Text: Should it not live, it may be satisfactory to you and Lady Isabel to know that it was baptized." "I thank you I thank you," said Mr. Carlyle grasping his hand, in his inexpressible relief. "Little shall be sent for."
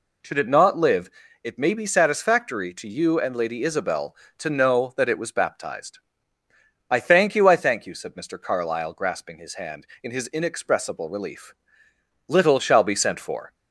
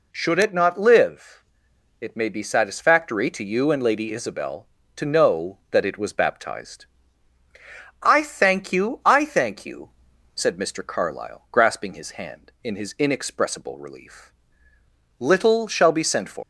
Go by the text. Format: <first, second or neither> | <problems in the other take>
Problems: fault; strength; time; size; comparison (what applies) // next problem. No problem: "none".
first | leaves "for" unfinished; at 16.4 s; 155 ms